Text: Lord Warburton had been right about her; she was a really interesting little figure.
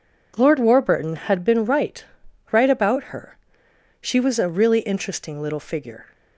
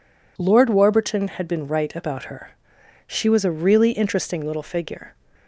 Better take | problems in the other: second | says "right" twice; at 2.5 s

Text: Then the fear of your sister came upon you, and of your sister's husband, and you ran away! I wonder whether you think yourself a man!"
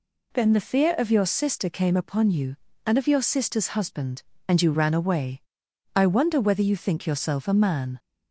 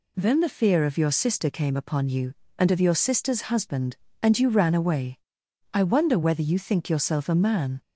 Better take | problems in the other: neither | none

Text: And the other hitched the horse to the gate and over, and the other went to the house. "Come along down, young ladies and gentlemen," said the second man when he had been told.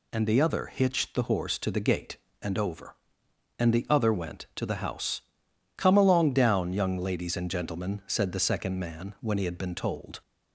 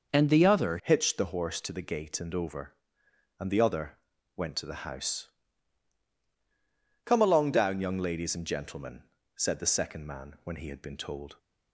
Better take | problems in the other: first | changes voice at "hitched"; from 0.8 s on; 10.5 s long // pauses between "other" and "went"; at 3.9 s; 0.38 s long

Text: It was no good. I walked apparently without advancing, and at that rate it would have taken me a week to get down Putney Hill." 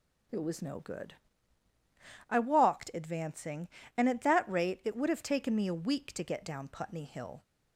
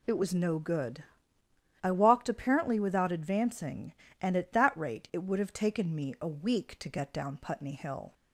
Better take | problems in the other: second | skips "apparently without"; at 2.9 s

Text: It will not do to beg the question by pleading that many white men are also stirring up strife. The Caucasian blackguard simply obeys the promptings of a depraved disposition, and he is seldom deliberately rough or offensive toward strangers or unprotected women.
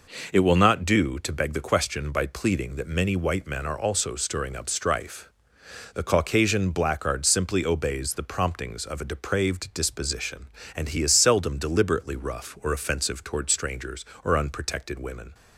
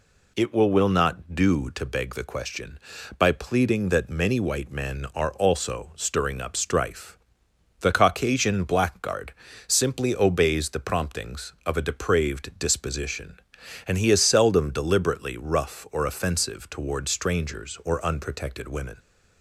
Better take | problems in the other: first | says "will" twice; at 0.6 s // pauses between "blackguard" and "simply"; slight; at 9.3 s; 0.34 s long

